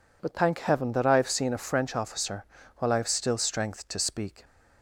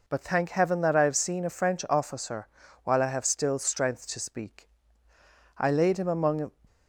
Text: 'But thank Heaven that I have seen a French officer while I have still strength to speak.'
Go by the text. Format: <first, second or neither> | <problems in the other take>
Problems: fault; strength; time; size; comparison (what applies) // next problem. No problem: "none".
first | pauses between "officer" and "while"; at 2.4 s; 0.38 s long; slight in the first // goes on to say "I laid him among"; noticeable; from 5.5 s on; 0.94 s long